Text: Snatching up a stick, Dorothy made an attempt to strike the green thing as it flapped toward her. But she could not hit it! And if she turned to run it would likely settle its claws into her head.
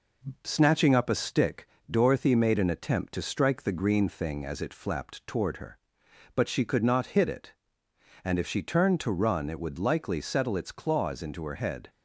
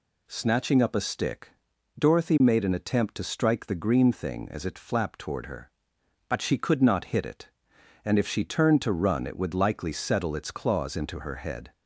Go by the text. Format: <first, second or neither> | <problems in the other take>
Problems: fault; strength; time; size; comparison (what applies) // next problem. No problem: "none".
second | gets quieter; slight; throughout; 2 dB